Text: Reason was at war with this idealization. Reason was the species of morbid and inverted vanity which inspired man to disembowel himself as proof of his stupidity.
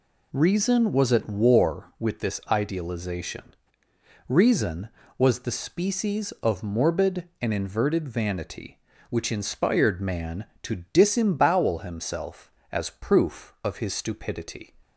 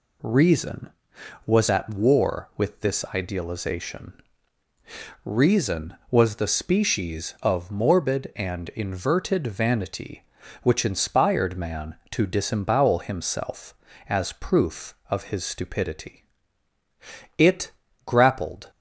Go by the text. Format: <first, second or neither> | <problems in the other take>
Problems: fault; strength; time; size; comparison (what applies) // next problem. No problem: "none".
first | goes on to say "It grappled"; from 17.3 s on; 1.3 s long